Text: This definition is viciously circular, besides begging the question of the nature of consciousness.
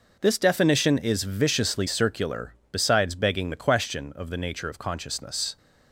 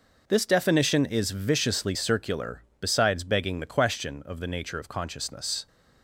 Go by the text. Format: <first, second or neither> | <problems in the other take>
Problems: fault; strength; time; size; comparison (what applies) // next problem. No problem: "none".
neither | none